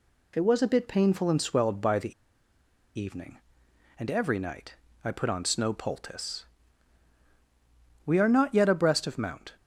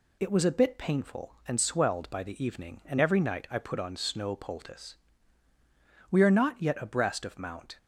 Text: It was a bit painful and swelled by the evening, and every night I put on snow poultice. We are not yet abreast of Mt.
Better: second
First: pauses between "the" and "evening"; noticeable; at 2.1 s; 0.84 s long // pauses between "night" and "I"; slight; at 4.7 s; 0.28 s long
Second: none

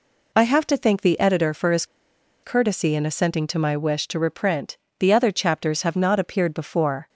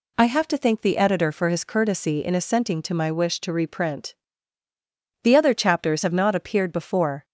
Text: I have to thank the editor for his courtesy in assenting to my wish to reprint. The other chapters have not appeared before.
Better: second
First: pauses between "his" and "courtesy"; noticeable; at 1.8 s; 0.59 s long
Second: none

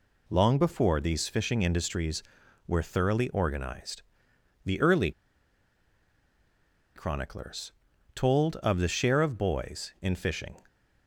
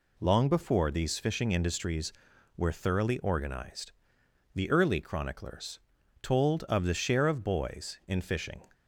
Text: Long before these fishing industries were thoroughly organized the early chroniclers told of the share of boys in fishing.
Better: second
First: pauses between "organized" and "the"; noticeable; at 4.0 s; 0.62 s long // pauses between "early" and "chroniclers"; strong; at 5.1 s; 1.8 s long // pauses between "chroniclers" and "told"; at 7.7 s; 0.44 s long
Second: pauses between "organized" and "the"; noticeable; at 3.9 s; 0.62 s long // pauses between "chroniclers" and "told"; at 5.7 s; 0.44 s long

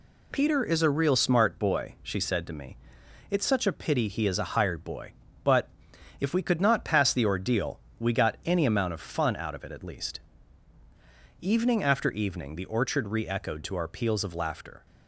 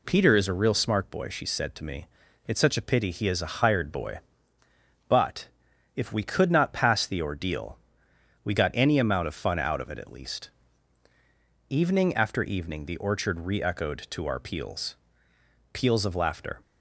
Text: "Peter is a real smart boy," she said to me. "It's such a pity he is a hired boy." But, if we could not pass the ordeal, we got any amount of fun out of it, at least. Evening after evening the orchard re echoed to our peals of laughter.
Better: first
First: none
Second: says "peals" twice; at 15.7 s

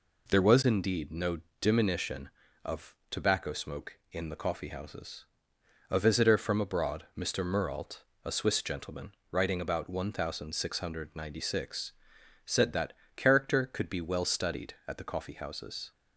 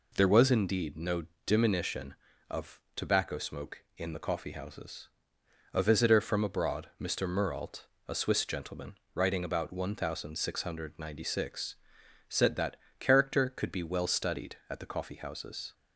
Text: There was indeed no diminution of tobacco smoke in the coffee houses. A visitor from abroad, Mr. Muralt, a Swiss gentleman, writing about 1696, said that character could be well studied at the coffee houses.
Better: neither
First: pauses between "no" and "diminution"; slight; at 1.3 s; 0.22 s long // pauses between "that" and "character"; slight; at 12.9 s; 0.24 s long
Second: pauses between "no" and "diminution"; slight; at 1.2 s; 0.22 s long // pauses between "that" and "character"; slight; at 12.7 s; 0.24 s long

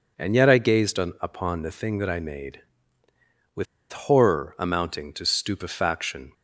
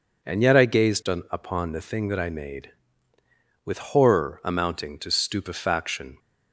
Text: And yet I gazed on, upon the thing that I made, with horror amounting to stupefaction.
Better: second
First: pauses between "with" and "horror"; slight; at 3.6 s; 0.27 s long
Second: none

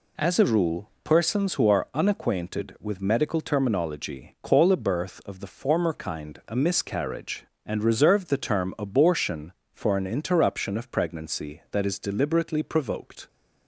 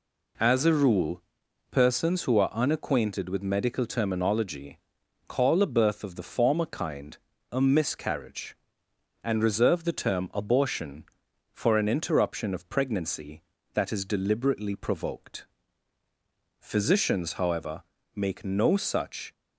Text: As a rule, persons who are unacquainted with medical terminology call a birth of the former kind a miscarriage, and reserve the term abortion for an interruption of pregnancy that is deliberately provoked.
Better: first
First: none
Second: pauses between "terminology" and "call"; noticeable; at 4.7 s; 0.50 s long // pauses between "kind" and "a"; slight; at 7.1 s; 0.34 s long // goes on to say "Physicians however make no such"; strong; from 16.6 s on; 2.7 s long

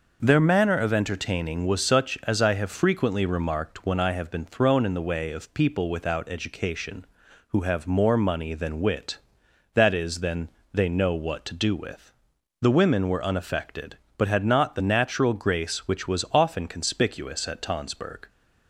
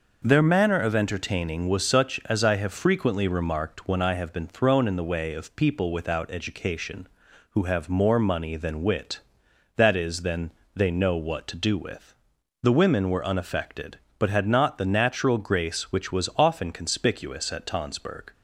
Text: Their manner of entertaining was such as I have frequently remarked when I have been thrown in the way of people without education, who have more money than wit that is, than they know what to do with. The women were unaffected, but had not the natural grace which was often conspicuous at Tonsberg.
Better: neither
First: pauses between "than" and "they"; slight; at 10.4 s; 0.24 s long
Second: pauses between "than" and "they"; slight; at 10.5 s; 0.24 s long

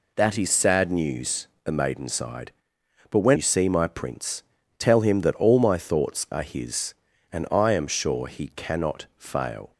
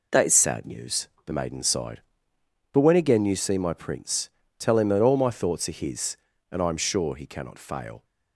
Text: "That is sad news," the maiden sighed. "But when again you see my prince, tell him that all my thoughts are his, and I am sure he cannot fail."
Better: second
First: skips "again"; at 3.3 s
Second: none

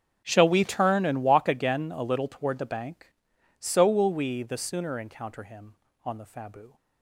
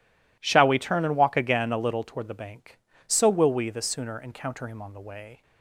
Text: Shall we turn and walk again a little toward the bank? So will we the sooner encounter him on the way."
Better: second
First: starts louder than the rest; until 1.2 s; 6.5 dB // says "fabu" for "way"; at 6.2 s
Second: none

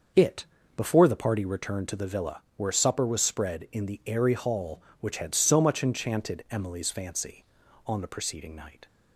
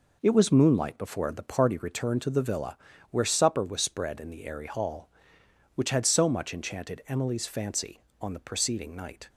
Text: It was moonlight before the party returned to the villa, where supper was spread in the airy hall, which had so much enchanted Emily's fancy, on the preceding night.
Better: second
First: starts louder than the rest; noticeable; until 1.4 s; 6 dB // skips "was moonlight"; at 0.6 s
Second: none

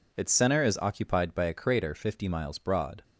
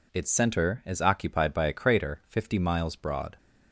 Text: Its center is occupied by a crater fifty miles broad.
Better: neither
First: none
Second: none

